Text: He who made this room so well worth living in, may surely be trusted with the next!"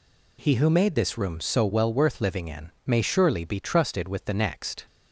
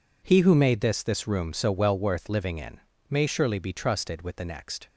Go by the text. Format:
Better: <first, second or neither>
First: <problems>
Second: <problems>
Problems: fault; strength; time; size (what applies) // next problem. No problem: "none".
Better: first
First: none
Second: says "this" twice; at 1.0 s